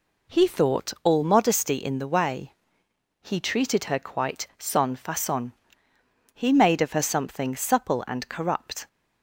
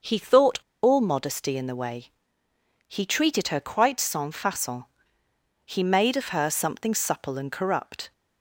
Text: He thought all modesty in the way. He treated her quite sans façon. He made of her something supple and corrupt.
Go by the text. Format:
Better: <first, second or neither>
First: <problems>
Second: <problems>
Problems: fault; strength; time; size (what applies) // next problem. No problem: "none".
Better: first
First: none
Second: starts louder than the rest; noticeable; until 1.2 s; 6 dB // pauses between "thought" and "all"; slight; at 0.5 s; 0.25 s long